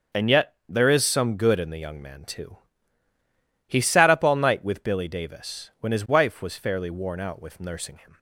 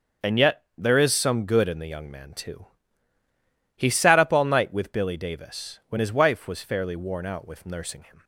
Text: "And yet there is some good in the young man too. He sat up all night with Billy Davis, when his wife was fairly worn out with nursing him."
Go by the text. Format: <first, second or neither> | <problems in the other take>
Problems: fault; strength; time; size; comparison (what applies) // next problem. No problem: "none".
neither | starts louder than the rest; the same in both